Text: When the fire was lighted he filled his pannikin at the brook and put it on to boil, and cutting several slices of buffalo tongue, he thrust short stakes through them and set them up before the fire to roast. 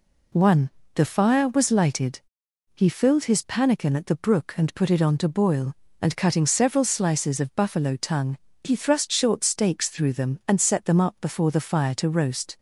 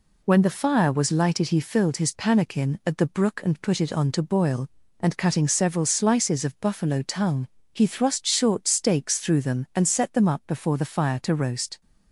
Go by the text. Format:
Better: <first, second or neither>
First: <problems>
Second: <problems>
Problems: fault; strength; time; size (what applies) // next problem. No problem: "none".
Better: second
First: says "One" for "When"; at 0.3 s // pauses between "lighted" and "he"; noticeable; at 2.1 s; 0.56 s long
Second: none